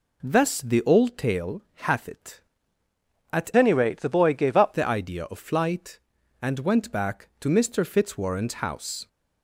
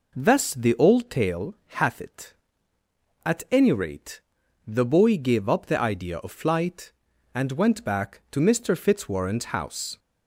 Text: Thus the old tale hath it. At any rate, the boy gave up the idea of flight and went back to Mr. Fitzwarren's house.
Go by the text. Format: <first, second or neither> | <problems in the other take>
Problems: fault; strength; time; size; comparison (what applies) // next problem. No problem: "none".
second | pauses between "tale" and "hath"; slight; at 1.6 s; 0.24 s long; slight in the second // changes voice from "any" to "up"; from 3.5 to 4.7 s; 1.2 s long